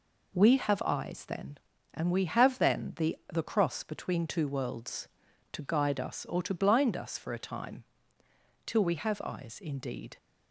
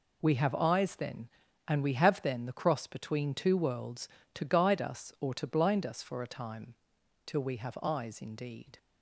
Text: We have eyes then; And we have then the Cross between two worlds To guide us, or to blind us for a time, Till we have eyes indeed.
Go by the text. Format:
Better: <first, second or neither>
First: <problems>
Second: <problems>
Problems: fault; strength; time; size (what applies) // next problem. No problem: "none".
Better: second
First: says "the" twice; at 3.3 s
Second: none